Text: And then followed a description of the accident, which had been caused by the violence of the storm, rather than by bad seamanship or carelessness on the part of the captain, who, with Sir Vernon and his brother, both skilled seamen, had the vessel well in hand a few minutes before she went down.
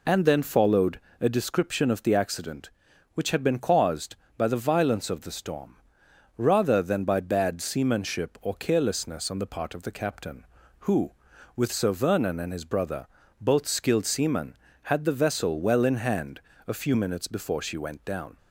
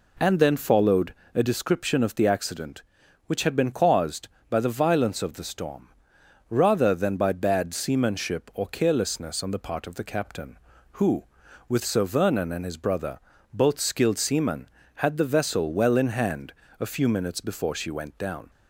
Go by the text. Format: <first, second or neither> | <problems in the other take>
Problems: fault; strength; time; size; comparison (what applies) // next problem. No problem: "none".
second | loses the start of "And"; at 0.0 s; 25 ms // pauses between "followed" and "a"; slight; at 0.9 s; 0.20 s long; slight in the second // pauses between "hand" and "a"; slight; at 16.4 s; 0.26 s long; slight in the second